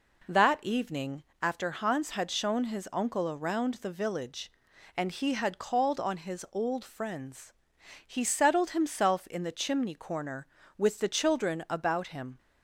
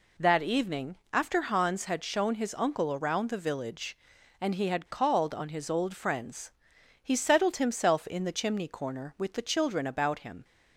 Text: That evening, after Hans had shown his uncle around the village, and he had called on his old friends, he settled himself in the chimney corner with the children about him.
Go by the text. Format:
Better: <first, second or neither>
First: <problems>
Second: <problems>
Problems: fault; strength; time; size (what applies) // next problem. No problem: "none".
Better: neither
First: none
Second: none